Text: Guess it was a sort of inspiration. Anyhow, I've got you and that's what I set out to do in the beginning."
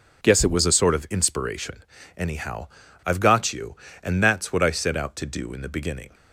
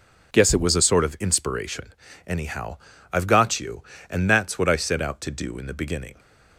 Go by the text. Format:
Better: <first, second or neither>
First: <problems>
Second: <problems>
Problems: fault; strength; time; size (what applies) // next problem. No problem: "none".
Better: neither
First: none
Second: none